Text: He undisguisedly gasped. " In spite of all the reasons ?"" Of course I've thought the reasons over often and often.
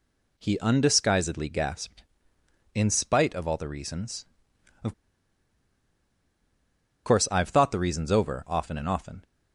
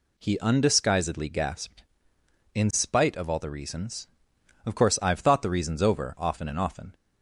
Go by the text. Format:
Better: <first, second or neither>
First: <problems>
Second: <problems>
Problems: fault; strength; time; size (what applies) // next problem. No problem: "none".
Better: second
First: pauses between "Of" and "course"; strong; at 4.9 s; 2.1 s long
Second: none